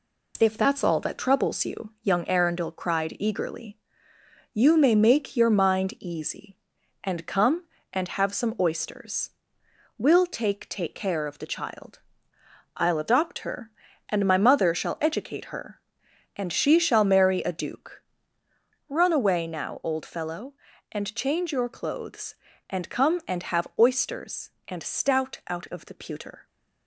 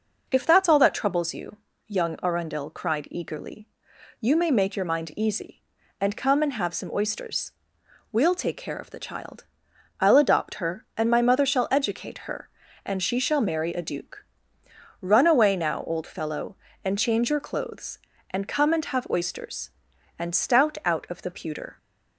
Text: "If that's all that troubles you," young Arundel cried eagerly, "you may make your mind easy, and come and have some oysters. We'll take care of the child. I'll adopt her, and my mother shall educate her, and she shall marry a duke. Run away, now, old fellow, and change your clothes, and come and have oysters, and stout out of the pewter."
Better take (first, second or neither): second